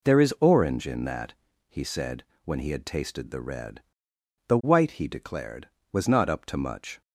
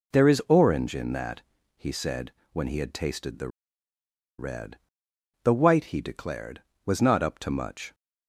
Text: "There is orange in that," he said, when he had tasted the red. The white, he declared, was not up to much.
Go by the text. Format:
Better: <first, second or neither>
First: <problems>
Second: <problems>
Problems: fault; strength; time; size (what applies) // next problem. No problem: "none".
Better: first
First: none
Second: pauses between "the" and "red"; noticeable; at 3.4 s; 0.90 s long